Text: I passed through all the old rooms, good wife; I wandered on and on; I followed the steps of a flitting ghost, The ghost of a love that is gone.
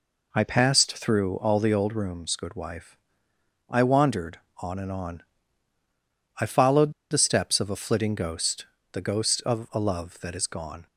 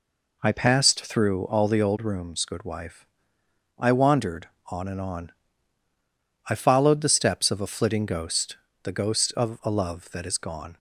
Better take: second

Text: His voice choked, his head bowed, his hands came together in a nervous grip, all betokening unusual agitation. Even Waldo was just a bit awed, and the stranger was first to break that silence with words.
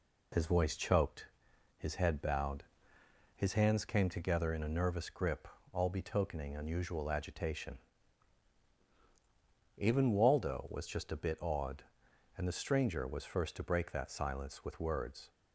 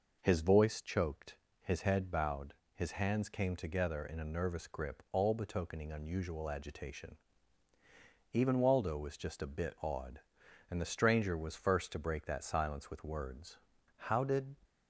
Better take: first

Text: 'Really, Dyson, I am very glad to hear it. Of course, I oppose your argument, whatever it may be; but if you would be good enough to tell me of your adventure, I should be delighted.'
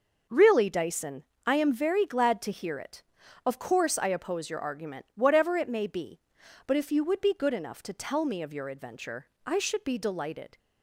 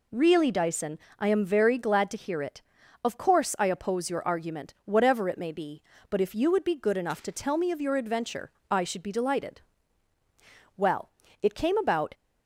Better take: first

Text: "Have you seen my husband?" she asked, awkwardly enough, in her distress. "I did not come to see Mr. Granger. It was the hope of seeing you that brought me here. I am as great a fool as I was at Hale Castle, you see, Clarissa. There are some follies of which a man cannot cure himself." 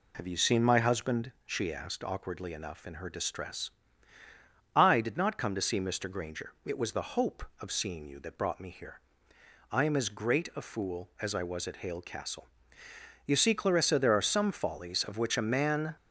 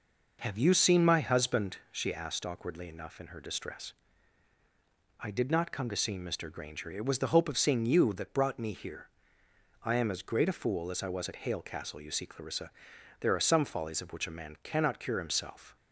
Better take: second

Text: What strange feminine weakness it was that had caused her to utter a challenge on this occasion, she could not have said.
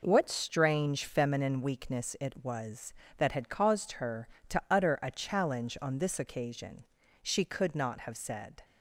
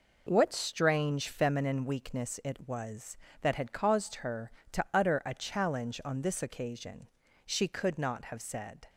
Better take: neither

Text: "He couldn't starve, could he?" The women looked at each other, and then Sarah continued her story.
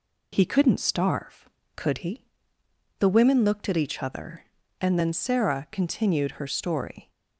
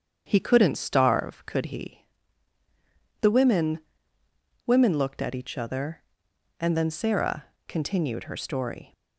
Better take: first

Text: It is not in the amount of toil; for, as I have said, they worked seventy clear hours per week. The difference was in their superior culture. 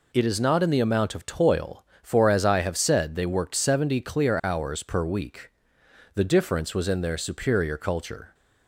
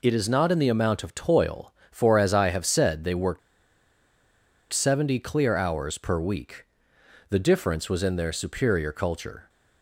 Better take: first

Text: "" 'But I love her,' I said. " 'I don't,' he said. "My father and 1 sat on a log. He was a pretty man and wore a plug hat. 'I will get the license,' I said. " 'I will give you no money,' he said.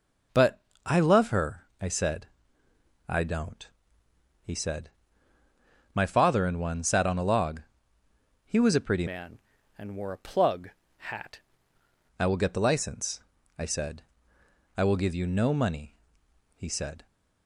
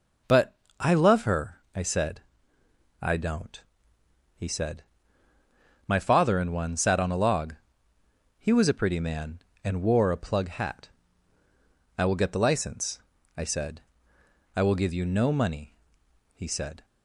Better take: second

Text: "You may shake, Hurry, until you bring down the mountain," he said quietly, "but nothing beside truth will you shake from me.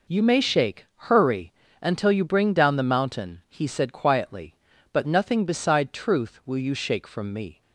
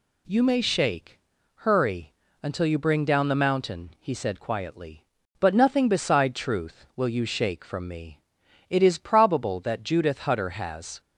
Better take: first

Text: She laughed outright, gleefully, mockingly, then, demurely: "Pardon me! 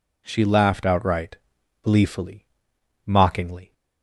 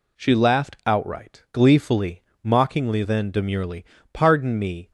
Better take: second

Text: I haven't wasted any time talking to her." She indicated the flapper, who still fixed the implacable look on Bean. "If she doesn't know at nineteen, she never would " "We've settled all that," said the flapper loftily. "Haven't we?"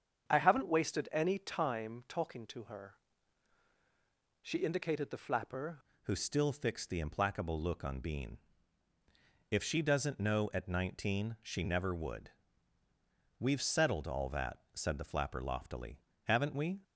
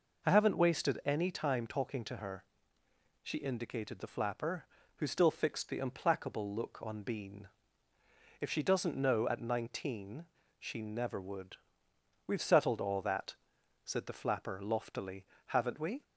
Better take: second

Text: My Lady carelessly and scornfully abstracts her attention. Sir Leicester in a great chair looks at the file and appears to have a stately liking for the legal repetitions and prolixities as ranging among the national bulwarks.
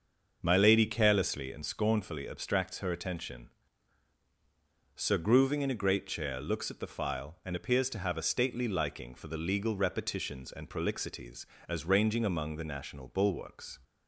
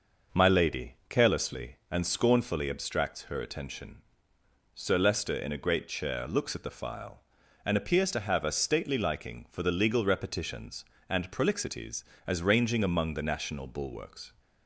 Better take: second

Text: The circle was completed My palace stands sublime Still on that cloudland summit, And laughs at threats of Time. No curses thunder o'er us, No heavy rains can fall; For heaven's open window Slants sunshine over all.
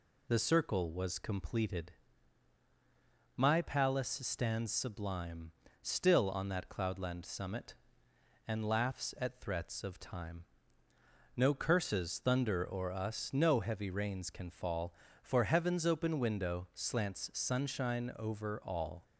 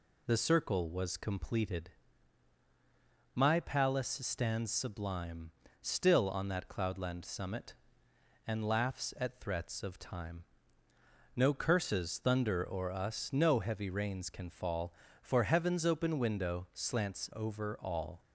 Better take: first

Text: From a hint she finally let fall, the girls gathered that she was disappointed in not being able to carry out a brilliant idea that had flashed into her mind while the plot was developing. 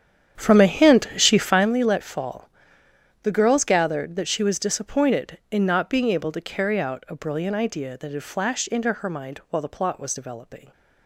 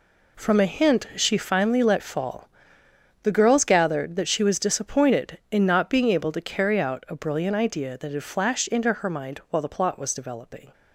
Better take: second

